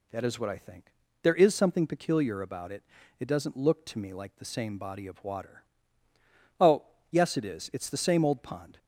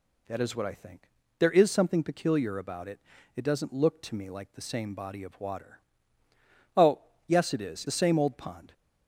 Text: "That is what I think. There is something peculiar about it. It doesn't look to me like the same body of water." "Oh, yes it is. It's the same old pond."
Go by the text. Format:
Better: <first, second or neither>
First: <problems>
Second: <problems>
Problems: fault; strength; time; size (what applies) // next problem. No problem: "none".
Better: first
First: none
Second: skips "It's"; at 7.8 s